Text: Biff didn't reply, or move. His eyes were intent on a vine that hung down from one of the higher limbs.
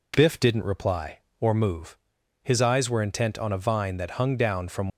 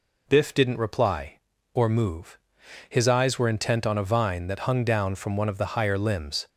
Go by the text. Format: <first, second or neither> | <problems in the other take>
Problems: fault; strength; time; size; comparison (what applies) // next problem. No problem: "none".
second | stops before "one of the higher limbs"; at 4.9 s